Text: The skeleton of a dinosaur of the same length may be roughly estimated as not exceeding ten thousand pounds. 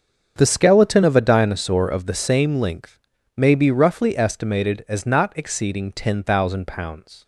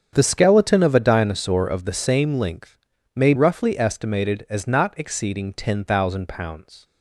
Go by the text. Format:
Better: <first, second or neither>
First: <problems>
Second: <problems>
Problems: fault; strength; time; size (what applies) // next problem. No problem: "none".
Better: first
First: starts louder than the rest; until 1.3 s; 7 dB // pauses between "length" and "may"; at 2.9 s; 0.38 s long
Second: starts louder than the rest; strong; until 1.1 s; 8 dB // pauses between "length" and "may"; at 2.7 s; 0.38 s long // skips "be"; at 3.3 s